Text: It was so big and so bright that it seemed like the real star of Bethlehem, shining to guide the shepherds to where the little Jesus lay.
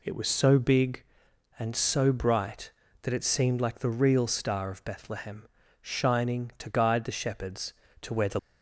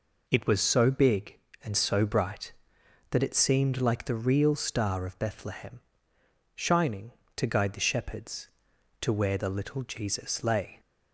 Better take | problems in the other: second | stops before "little Jesus lay"; at 8.3 s

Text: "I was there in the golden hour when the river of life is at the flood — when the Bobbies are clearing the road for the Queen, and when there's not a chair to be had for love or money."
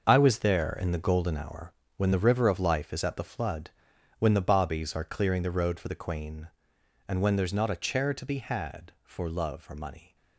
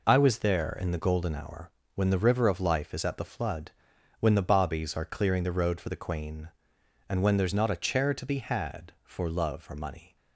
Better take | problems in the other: second | gets quieter; strong; throughout; 10.5 dB // pauses between "hour" and "when"; slight; at 1.7 s; 0.24 s long; slight in the second

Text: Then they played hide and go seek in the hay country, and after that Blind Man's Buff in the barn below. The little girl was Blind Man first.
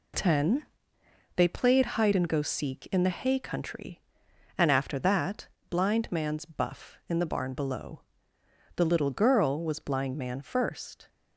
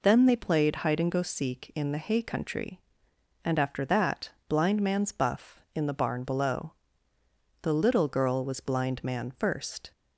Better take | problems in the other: second | says "Ten" for "Then"; at 0.1 s // pauses between "that" and "Blind"; slight; at 5.4 s; 0.22 s long; slight in the second

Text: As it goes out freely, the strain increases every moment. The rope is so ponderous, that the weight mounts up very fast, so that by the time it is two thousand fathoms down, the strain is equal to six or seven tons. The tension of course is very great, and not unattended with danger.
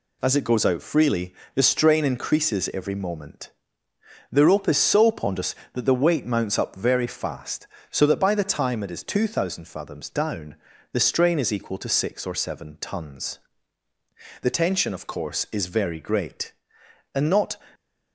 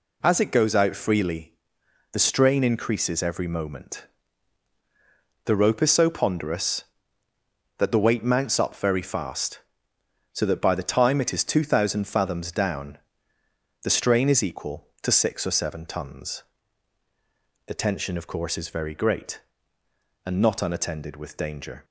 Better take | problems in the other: second | stops before "unattended with danger"; at 17.7 s

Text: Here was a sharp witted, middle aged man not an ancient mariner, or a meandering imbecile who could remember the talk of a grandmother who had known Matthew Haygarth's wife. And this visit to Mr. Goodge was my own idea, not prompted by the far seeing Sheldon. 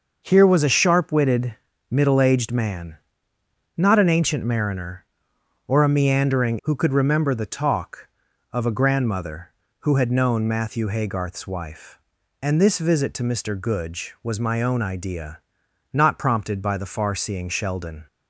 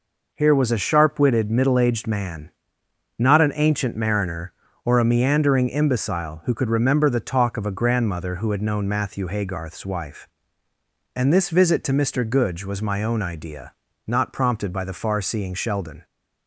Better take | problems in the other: second | starts louder than the rest; noticeable; until 1.2 s; 6 dB // pauses between "man" and "not"; noticeable; at 2.9 s; 0.78 s long; noticeable in the second // skips "imbecile"; at 6.5 s

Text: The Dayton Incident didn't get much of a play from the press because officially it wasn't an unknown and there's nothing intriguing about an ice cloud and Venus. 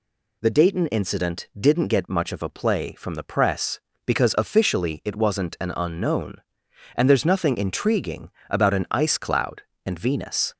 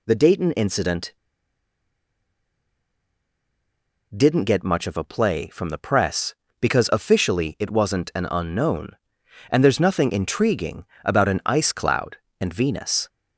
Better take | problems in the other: first | pauses between "Incident" and "didn't"; strong; at 1.1 s; 3.0 s long // pauses between "intriguing" and "about"; slight; at 10.8 s; 0.18 s long; slight in the first

